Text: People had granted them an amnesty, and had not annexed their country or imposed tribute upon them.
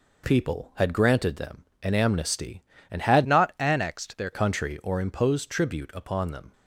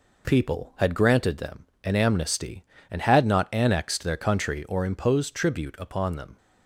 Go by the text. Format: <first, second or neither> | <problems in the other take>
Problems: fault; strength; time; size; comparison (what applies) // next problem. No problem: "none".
second | pauses between "them" and "an"; slight; at 1.6 s; 0.18 s long; slight in the second // changes voice from "not" to "their"; from 3.2 to 4.3 s; 1.1 s long